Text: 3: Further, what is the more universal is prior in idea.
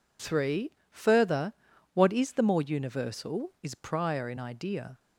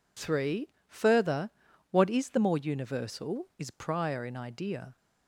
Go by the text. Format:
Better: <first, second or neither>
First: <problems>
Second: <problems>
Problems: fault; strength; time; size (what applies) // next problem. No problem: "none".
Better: neither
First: none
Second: none